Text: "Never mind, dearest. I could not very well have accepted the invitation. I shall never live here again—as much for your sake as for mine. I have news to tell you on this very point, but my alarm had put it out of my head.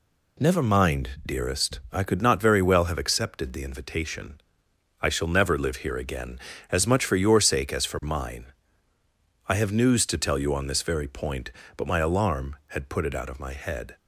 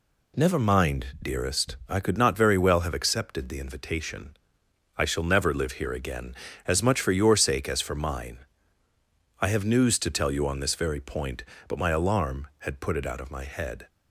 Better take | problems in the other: neither | none

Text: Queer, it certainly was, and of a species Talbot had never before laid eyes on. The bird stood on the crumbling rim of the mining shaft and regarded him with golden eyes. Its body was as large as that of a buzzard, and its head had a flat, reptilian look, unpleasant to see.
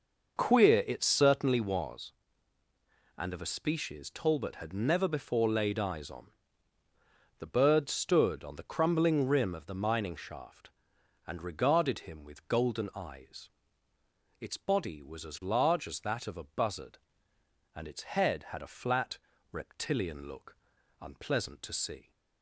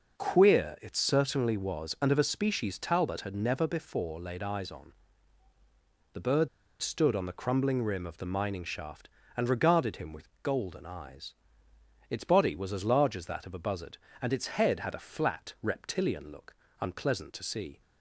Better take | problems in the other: first | pauses between "bird" and "stood"; slight; at 6.4 s; 0.32 s long

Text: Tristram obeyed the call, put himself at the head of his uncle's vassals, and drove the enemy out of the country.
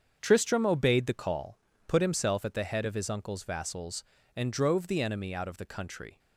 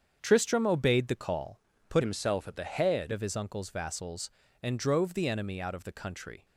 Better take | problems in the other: first | starts louder than the rest; strong; until 1.2 s; 7.5 dB; strong in the first // changes voice from "himself" to "head"; from 2.0 to 3.1 s; 1.1 s long

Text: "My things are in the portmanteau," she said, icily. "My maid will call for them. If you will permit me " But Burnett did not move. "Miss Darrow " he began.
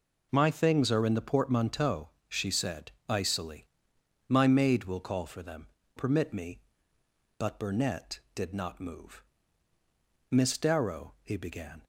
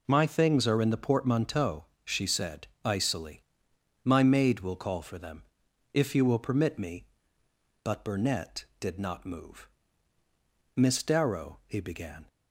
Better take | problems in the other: second | skips "If you will"; at 5.8 s

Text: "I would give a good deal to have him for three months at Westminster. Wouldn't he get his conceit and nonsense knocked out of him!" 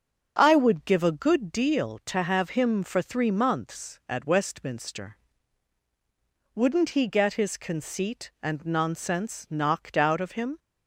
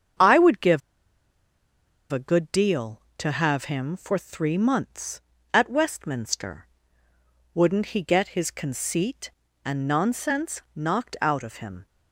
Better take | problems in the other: first | starts louder than the rest; strong; until 2.5 s; 7.5 dB; also in the first // pauses between "give" and "a"; strong; at 0.8 s; 1.3 s long

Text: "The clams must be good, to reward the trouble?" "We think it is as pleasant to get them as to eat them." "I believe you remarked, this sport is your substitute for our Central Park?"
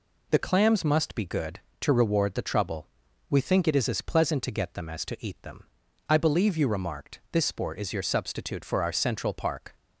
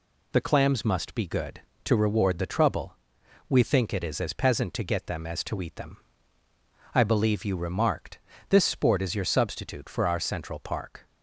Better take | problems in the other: first | says "peasant" for "pleasant"; at 4.3 s

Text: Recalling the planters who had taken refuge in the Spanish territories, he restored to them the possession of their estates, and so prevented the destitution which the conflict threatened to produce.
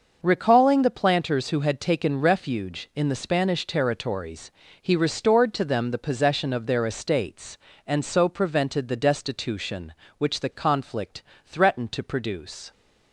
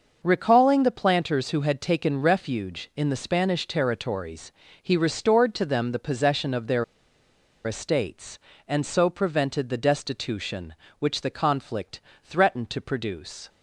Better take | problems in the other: first | starts louder than the rest; until 1.2 s; 6 dB; noticeable in the first // pauses between "their" and "estates"; noticeable; at 6.8 s; 0.82 s long // pauses between "conflict" and "threatened"; slight; at 11.9 s; 0.24 s long; slight in the first

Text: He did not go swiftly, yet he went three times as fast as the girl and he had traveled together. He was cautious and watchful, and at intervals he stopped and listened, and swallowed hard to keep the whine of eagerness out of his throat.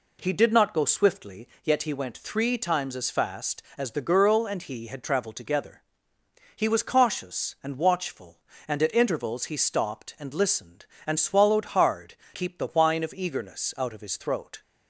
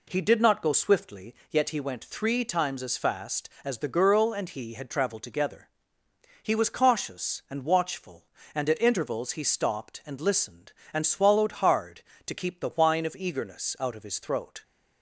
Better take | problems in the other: second | skips "to"; at 12.2 s

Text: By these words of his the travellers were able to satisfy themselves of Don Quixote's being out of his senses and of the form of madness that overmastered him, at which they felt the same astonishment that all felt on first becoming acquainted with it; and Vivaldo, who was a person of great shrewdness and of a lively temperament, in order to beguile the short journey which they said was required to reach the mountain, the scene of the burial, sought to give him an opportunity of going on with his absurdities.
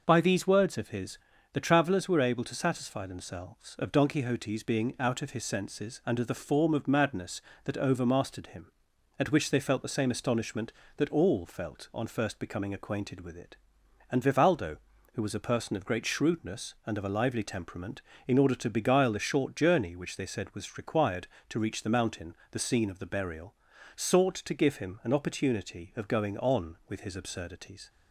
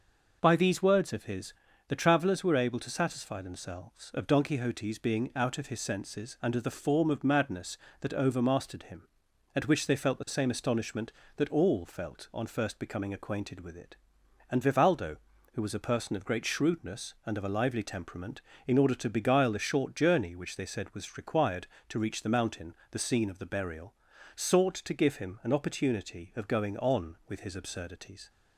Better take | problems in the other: neither | pauses between "his" and "the"; slight; the same in both

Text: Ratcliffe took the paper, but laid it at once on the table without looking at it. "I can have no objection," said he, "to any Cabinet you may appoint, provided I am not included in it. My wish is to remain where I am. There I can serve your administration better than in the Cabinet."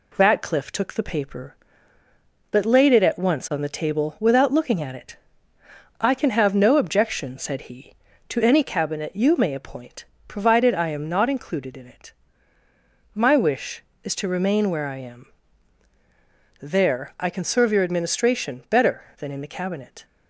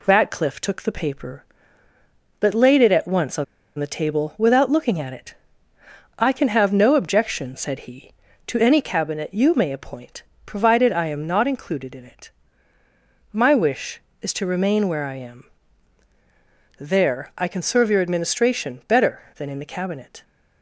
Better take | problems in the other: first | pauses between "on" and "the"; slight; at 3.4 s; 0.33 s long

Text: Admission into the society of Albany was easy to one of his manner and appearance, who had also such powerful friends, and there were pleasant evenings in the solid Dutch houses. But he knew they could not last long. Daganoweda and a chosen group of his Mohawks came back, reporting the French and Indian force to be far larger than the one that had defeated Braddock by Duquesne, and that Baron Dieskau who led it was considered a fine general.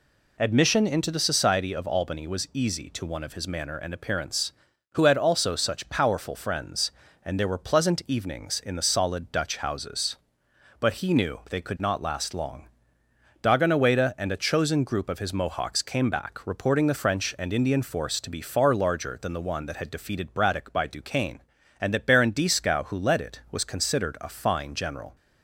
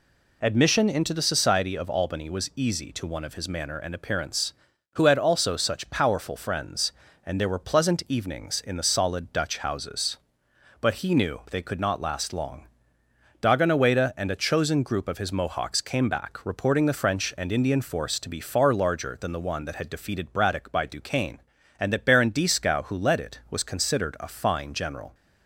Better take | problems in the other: neither | none

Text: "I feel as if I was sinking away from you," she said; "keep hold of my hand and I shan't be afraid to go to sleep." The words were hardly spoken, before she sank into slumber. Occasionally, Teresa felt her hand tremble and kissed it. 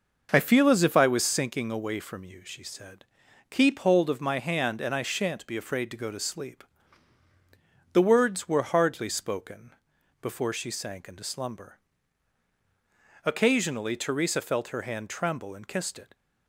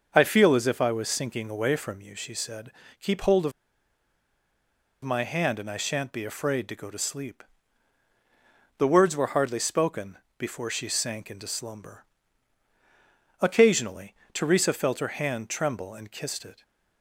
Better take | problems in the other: first | starts louder than the rest; noticeable; until 1.1 s; 6 dB // pauses between "of" and "my"; strong; at 3.5 s; 1.5 s long

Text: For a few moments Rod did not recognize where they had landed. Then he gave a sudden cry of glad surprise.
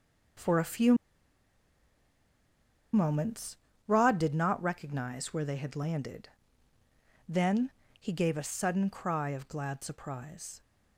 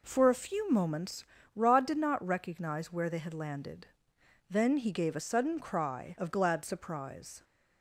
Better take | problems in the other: second | pauses between "few" and "moments"; strong; at 0.9 s; 1.9 s long // pauses between "moments" and "Rod"; slight; at 3.5 s; 0.32 s long; slight in the second // pauses between "Then" and "he"; slight; at 7.7 s; 0.30 s long

